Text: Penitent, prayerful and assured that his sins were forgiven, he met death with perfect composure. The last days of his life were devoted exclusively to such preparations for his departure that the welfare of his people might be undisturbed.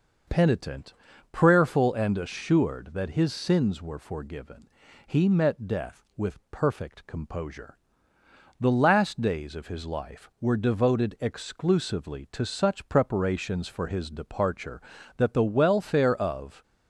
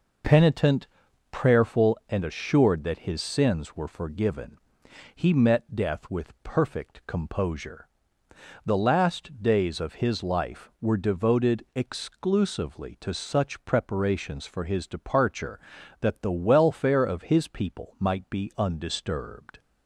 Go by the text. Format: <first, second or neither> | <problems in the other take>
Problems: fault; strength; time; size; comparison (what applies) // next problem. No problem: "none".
second | stops before "his people might be undisturbed"; at 16.6 s